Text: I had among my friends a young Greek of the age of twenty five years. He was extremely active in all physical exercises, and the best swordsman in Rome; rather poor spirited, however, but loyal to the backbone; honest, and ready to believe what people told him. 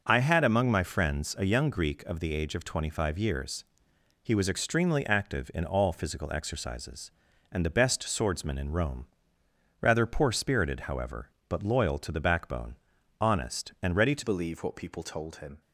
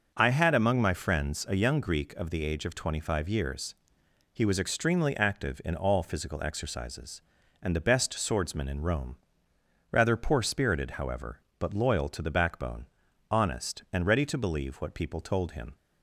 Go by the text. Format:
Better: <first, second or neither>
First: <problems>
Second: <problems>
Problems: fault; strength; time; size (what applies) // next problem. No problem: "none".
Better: second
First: changes voice at "believe"; from 14.2 s on; 1.4 s long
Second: none